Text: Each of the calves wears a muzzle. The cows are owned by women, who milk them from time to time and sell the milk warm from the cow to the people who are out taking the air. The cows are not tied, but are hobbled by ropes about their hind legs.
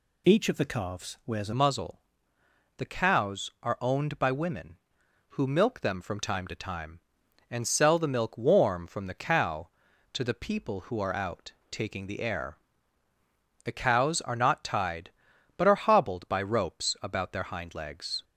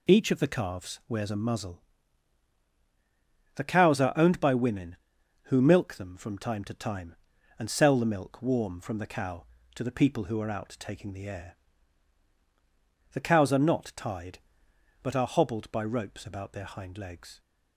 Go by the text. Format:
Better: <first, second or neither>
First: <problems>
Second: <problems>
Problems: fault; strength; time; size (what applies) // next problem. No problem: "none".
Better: second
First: changes voice at "muzzle"; from 1.5 s on; 16.7 s long // pauses between "out" and "taking"; slight; at 11.5 s; 0.18 s long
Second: none